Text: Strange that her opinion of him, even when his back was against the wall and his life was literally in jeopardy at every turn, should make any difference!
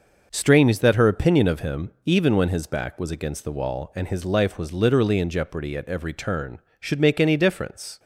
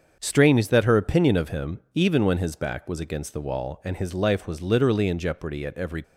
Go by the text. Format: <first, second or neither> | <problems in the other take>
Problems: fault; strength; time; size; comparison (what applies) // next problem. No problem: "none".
first | starts louder than the rest; until 1.2 s; 7 dB // stops before "turn should make any difference"; at 6.0 s